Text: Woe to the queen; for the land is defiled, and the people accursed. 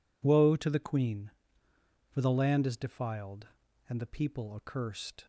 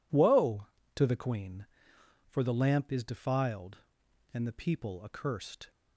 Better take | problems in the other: first | says "lamp" for "land"; at 2.5 s

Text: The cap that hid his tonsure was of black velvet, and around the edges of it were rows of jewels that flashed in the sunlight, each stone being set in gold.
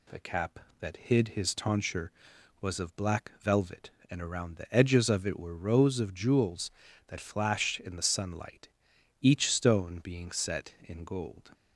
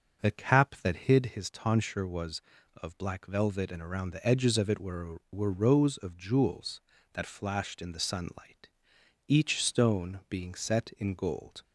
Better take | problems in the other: first | starts louder than the rest; until 1.2 s; 6.5 dB // says "were" twice; at 5.3 s

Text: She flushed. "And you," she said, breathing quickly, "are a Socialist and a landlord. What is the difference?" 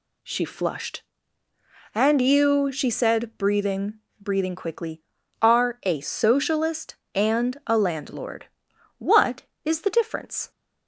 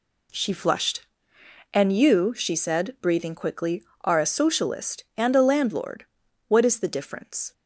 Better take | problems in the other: second | says "breathing" twice; at 4.2 s

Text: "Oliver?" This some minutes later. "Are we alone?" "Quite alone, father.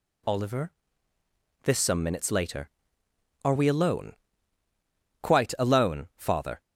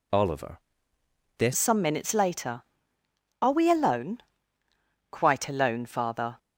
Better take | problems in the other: first | changes voice at "some"; from 1.5 s on; 4.8 s long

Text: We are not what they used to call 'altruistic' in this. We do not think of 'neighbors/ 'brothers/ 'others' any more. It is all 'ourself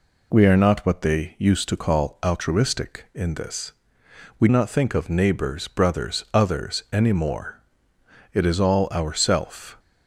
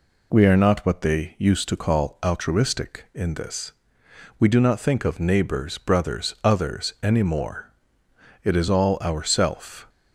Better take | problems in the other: second | skips "do"; at 4.4 s

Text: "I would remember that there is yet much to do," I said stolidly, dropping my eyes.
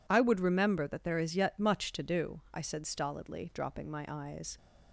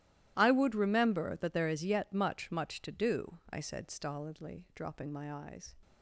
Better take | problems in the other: first | starts louder than the rest; strong; until 1.3 s; 14.5 dB // says "much" twice; at 2.5 s

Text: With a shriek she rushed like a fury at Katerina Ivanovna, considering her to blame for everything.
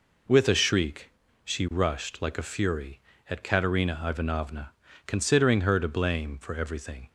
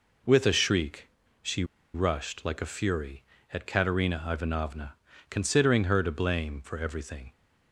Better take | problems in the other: first | pauses between "shriek" and "she"; slight; at 1.0 s; 0.34 s long; slight in the first // pauses between "she" and "rushed"; slight; at 1.6 s; 0.28 s long

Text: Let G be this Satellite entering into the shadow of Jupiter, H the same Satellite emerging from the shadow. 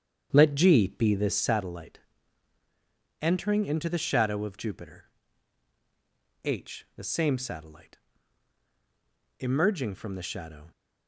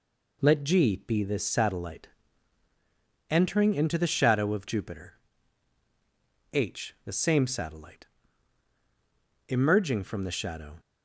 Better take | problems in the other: second | starts louder than the rest; strong; until 1.6 s; 8.5 dB // pauses between "Satellite" and "entering"; at 1.9 s; 1.2 s long; also in the second // pauses between "Satellite" and "emerging"; strong; at 7.9 s; 1.4 s long; strong in the second

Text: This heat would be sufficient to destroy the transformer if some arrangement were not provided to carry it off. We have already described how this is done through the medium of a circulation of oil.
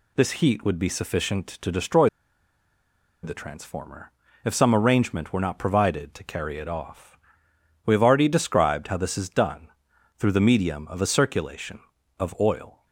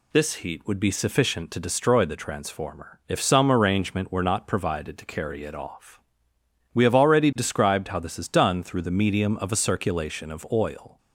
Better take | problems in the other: second | pauses between "destroy" and "the"; at 2.0 s; 1.1 s long // pauses between "transformer" and "if"; slight; at 4.1 s; 0.32 s long // pauses between "done" and "through"; noticeable; at 9.6 s; 0.48 s long

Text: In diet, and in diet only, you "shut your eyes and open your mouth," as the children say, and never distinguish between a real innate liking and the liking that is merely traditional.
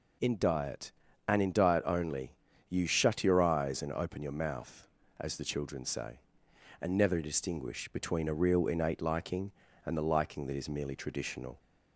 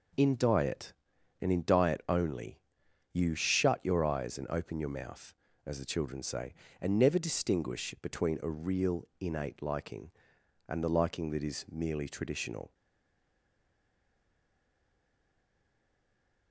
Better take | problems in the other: first | stays silent after the last word; strong; from 12.7 s on; 3.8 s long

